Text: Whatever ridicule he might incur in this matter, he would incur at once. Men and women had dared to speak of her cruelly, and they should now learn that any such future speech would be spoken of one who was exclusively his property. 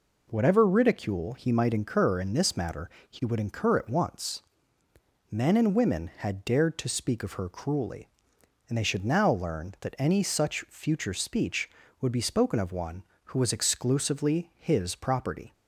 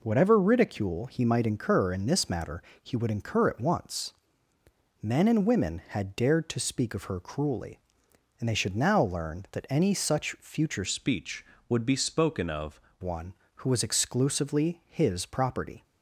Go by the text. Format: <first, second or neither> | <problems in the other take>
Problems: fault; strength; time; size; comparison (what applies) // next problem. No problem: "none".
first | changes voice from "speech" to "of"; from 10.8 to 12.7 s; 1.9 s long